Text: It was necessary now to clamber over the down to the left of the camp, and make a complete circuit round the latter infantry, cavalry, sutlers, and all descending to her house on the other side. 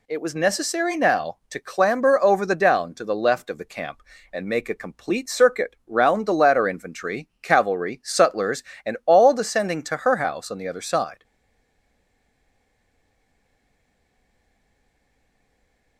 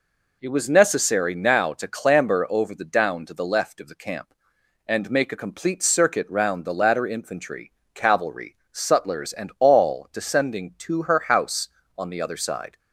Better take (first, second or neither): second